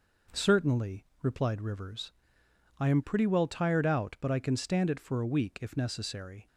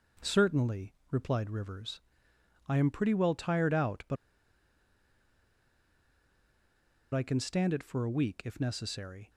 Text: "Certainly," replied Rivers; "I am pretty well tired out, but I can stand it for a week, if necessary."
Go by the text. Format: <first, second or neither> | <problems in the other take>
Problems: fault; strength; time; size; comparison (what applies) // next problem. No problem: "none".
first | pauses between "but" and "I"; strong; at 4.1 s; 2.9 s long